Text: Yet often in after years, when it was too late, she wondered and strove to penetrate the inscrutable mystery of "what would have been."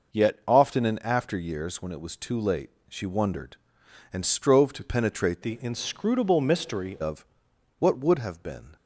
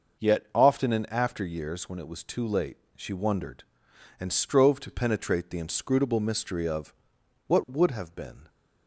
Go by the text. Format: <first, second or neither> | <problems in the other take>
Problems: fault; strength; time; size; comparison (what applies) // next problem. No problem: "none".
second | changes voice from "the" to "mystery"; from 5.4 to 6.9 s; 1.5 s long // pauses between "of" and "what"; noticeable; at 7.2 s; 0.54 s long; noticeable in the second